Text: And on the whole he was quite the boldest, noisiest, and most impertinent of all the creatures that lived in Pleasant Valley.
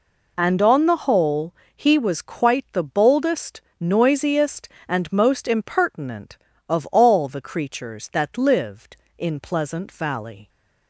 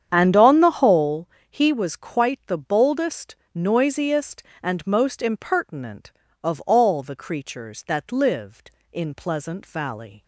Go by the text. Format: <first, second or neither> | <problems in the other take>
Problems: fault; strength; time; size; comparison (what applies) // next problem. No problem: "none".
first | starts louder than the rest; strong; until 1.2 s; 8.5 dB // pauses between "whole" and "he"; slight; at 1.2 s; 0.20 s long; slight in the first